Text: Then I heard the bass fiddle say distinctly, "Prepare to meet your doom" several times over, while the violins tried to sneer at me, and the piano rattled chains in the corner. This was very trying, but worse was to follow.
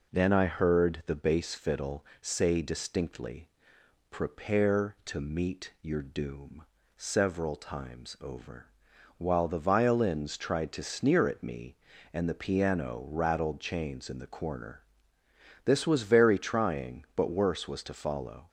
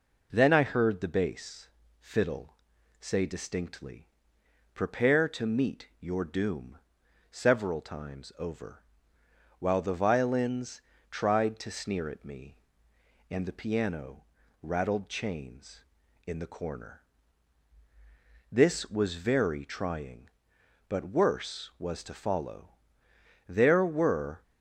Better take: first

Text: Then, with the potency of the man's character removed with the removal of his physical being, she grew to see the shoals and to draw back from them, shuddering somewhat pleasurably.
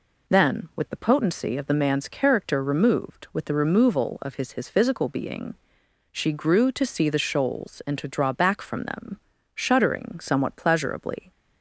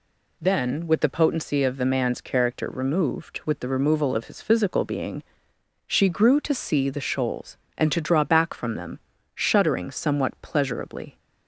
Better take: second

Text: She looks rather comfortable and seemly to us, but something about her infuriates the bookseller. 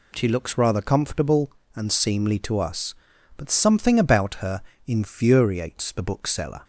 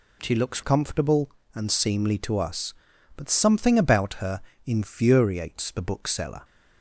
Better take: first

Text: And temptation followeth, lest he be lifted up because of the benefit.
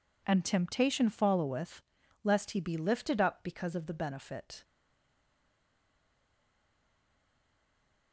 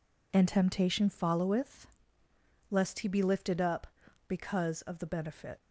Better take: second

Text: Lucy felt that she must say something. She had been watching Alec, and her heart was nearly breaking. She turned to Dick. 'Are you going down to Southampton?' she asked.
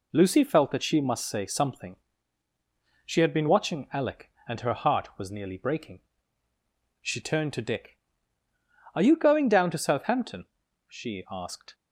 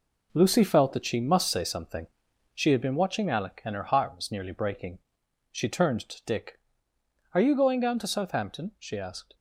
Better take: first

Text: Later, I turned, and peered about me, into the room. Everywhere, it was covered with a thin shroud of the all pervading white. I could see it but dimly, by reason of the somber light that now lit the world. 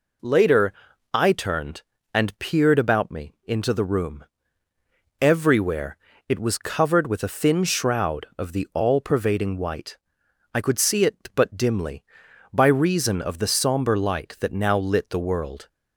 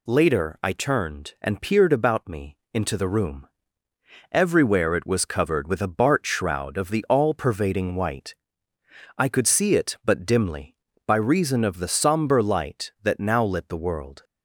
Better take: first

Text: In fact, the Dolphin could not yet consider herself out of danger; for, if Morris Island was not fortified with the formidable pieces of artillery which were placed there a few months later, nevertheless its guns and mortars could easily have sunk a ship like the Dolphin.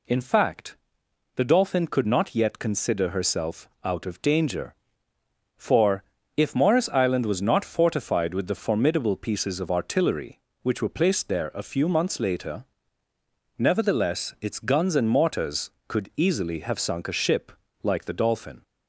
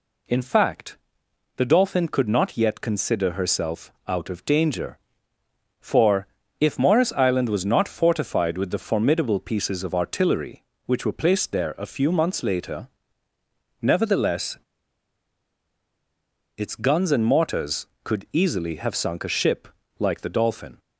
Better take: first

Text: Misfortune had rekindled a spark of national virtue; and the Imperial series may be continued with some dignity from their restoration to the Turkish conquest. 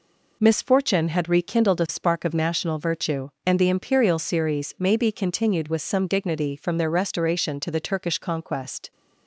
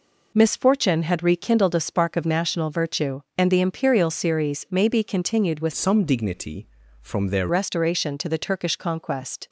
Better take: first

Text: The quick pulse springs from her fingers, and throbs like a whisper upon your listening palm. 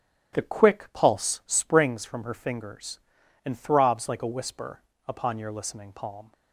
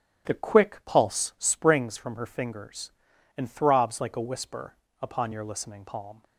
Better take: neither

